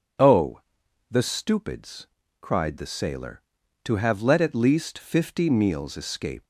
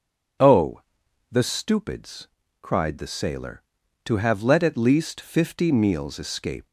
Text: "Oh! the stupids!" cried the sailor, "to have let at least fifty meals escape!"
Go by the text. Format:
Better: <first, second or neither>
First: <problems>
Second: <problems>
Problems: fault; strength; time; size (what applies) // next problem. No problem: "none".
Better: neither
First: none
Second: none